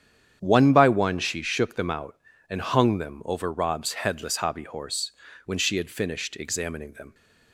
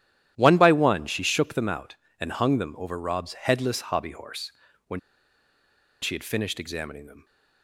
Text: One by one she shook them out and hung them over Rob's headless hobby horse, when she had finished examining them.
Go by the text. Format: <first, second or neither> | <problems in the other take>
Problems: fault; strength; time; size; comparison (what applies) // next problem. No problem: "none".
first | starts louder than the rest; strong; until 1.3 s; 12 dB; strong in the first // pauses between "when" and "she"; at 4.9 s; 1.0 s long